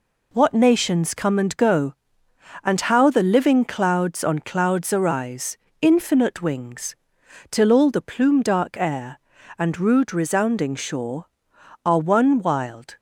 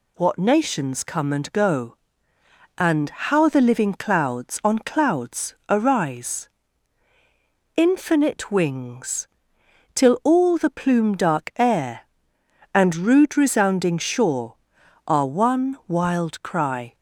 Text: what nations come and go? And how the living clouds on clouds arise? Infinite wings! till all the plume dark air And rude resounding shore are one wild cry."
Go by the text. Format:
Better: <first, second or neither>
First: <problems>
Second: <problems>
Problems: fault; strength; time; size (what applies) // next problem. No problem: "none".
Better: second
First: stops before "cry"; at 12.9 s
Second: none